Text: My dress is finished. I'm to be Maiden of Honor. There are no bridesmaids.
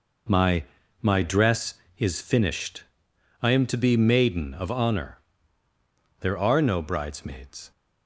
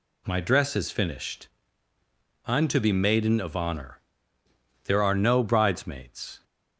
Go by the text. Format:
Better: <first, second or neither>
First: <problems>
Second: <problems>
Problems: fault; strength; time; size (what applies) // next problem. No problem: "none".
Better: second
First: says "My" twice; at 1.0 s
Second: none